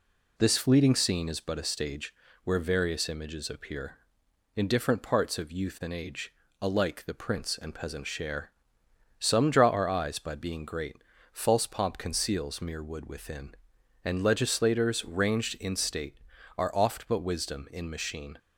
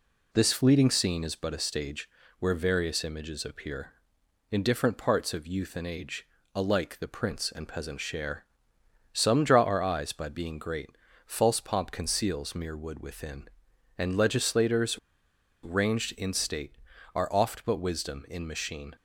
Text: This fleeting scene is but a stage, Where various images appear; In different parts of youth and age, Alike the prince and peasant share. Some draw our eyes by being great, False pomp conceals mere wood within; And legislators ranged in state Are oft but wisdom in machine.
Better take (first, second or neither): first